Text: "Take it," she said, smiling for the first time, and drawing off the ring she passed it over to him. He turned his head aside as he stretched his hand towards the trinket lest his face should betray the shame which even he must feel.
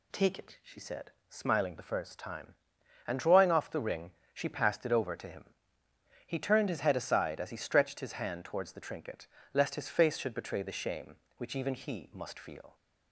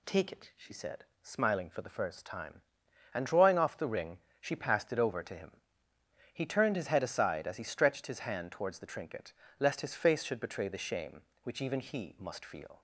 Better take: second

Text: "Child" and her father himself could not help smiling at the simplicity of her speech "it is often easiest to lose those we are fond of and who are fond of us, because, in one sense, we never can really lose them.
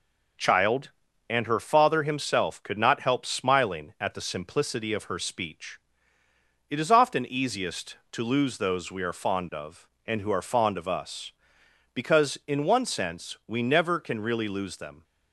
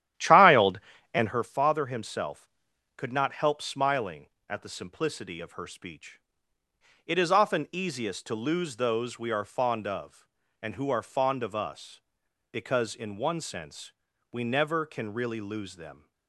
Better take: first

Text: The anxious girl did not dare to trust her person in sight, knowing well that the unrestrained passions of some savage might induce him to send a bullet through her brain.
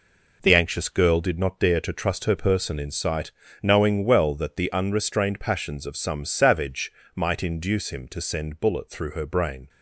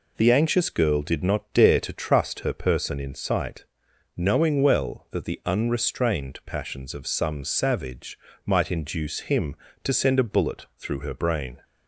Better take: second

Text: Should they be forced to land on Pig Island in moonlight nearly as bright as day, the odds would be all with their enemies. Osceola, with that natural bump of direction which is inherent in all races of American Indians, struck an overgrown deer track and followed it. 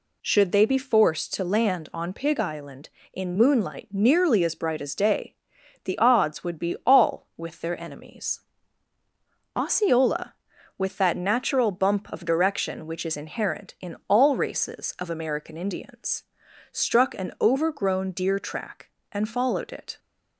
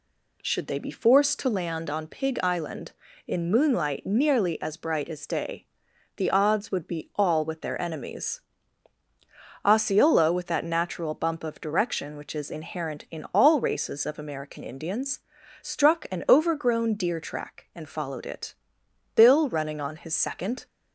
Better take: first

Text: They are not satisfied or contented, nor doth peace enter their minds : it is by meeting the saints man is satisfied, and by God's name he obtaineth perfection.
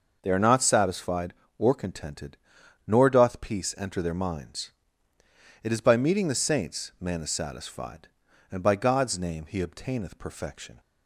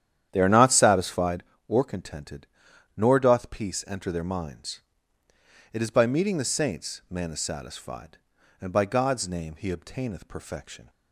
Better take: first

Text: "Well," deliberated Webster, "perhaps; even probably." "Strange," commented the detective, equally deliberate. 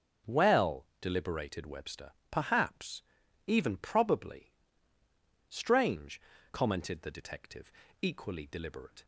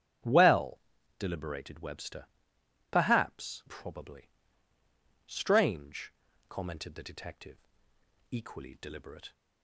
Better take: first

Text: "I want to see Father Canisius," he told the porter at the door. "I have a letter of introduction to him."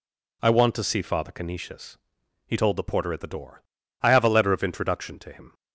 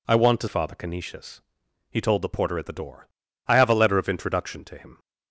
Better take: first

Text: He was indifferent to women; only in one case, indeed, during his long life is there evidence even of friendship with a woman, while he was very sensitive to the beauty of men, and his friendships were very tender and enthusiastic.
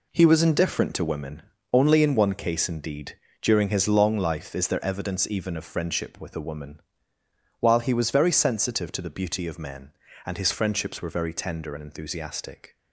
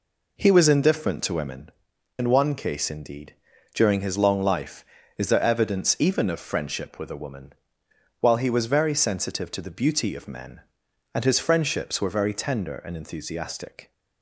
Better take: first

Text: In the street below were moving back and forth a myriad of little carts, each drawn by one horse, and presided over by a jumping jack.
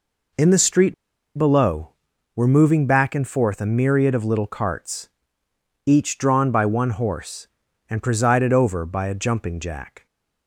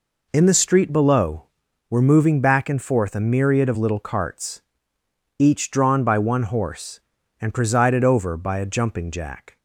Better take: second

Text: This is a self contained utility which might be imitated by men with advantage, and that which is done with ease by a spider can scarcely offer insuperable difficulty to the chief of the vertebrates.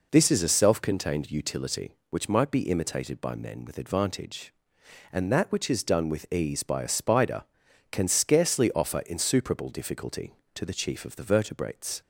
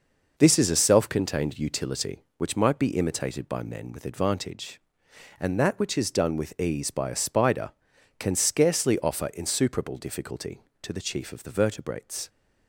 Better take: first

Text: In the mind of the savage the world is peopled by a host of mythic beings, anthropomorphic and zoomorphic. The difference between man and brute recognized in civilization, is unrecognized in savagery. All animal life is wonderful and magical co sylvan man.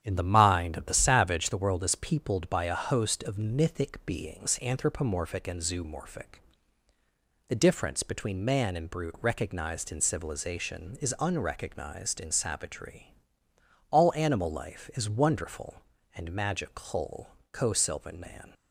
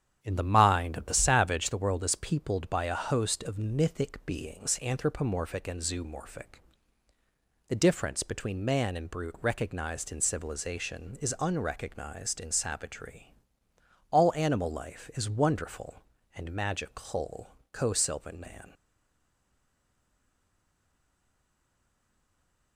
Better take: first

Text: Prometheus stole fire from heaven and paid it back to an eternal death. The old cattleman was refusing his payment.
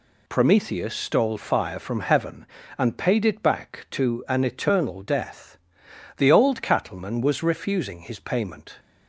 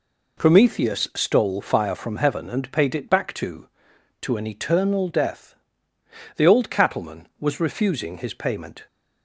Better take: first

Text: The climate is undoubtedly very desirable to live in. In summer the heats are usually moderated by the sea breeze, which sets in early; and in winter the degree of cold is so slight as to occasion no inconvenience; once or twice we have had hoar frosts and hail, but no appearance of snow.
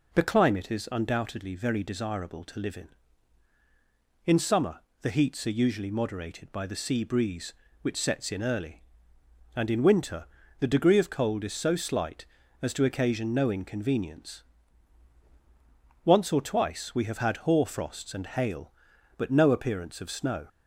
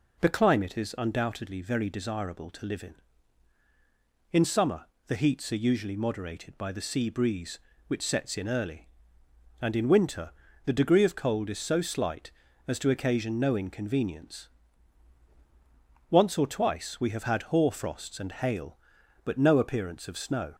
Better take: neither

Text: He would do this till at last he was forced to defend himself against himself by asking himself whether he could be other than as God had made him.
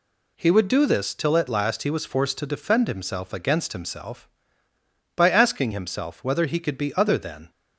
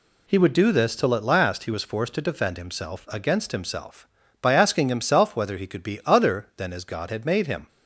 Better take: second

